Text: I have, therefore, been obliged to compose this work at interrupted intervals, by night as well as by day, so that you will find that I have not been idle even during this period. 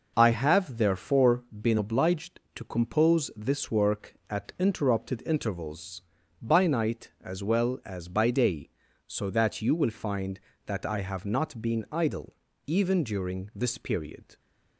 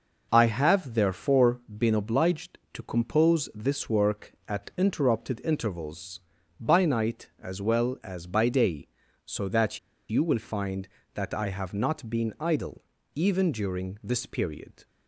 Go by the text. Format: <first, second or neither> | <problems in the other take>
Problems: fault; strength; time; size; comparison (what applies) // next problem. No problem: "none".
first | pauses between "that" and "you"; slight; at 9.7 s; 0.30 s long // pauses between "idle" and "even"; slight; at 12.8 s; 0.34 s long; slight in the first